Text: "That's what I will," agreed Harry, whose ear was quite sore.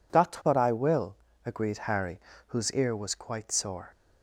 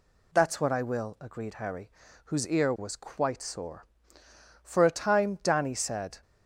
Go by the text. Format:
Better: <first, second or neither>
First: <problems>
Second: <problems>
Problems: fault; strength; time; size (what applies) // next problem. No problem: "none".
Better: first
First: none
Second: goes on to say "For a time Danny said"; from 4.6 s on; 1.5 s long